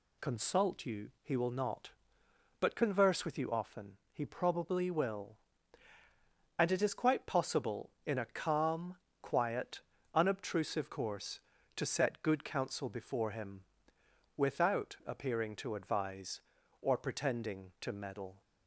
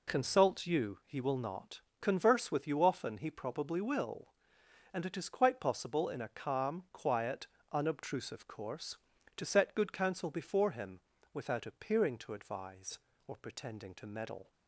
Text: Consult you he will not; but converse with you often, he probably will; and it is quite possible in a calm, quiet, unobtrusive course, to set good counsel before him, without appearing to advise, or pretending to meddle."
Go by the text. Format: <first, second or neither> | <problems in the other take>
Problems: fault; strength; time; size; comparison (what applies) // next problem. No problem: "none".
first | skips "but"; at 1.9 s